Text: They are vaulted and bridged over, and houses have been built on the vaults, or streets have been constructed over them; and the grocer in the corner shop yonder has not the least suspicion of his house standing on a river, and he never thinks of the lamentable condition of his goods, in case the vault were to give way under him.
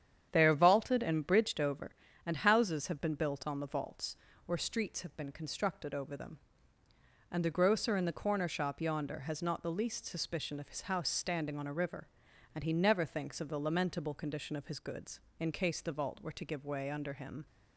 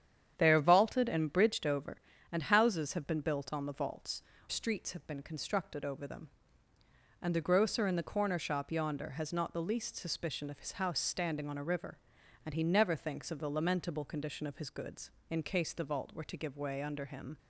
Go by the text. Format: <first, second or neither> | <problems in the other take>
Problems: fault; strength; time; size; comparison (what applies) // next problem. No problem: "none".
first | starts louder than the rest; strong; until 1.3 s; 9 dB; strong in the first // skips "or"; at 4.3 s